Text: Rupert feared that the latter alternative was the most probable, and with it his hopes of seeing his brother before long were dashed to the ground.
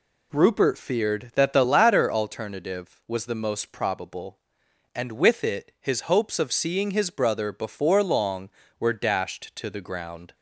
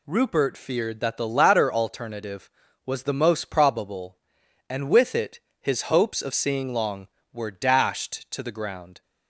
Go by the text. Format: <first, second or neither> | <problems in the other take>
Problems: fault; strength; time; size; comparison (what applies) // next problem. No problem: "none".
first | pauses between "it" and "his"; slight; at 5.4 s; 0.20 s long // skips "his brother before"; at 6.7 s